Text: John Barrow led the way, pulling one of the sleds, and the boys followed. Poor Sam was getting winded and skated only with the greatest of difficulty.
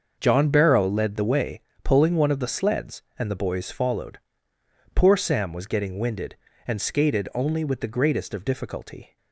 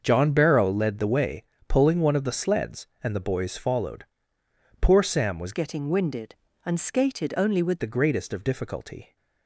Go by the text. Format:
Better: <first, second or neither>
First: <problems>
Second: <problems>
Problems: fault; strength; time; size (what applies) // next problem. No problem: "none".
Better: first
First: starts louder than the rest; until 1.2 s; 6.5 dB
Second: starts louder than the rest; until 1.0 s; 6.5 dB // changes voice from "getting" to "with"; from 5.5 to 7.8 s; 2.3 s long